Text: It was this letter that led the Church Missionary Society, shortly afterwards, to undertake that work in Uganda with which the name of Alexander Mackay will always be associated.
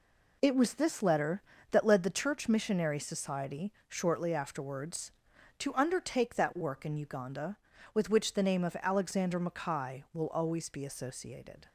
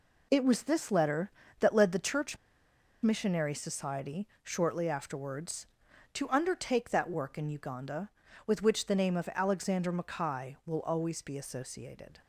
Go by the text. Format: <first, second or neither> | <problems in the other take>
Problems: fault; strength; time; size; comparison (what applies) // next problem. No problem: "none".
first | pauses between "Church" and "Missionary"; noticeable; at 2.3 s; 0.66 s long